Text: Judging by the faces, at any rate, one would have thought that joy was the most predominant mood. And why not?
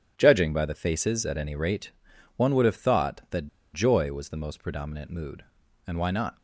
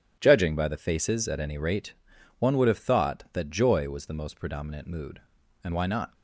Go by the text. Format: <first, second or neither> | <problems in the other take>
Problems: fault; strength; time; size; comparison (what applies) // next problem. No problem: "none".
second | pauses between "that" and "joy"; slight; at 3.4 s; 0.26 s long